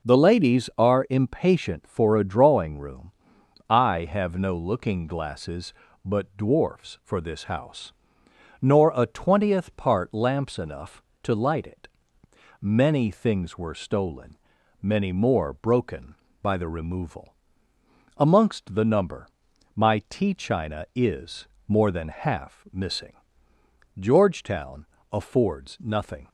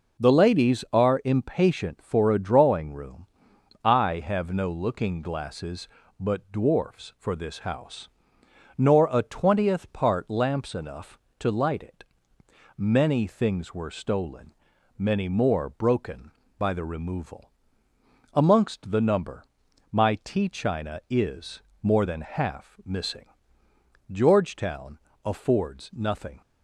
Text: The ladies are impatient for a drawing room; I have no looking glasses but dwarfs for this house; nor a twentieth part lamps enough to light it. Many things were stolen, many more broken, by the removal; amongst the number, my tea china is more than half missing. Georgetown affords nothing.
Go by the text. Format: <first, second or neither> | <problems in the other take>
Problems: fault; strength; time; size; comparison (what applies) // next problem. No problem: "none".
neither | pauses between "is" and "more"; slight; the same in both // pauses between "Georgetown" and "affords"; slight; the same in both